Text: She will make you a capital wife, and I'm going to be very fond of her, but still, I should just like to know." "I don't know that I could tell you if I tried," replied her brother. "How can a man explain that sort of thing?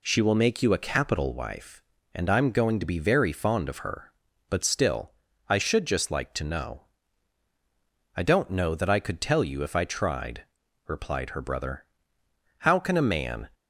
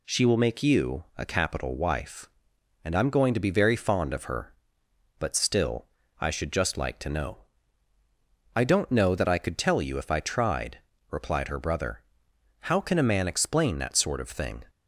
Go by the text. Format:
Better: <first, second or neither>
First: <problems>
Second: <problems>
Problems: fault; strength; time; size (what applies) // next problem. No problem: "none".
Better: second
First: stops before "explain that sort of thing"; at 13.5 s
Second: none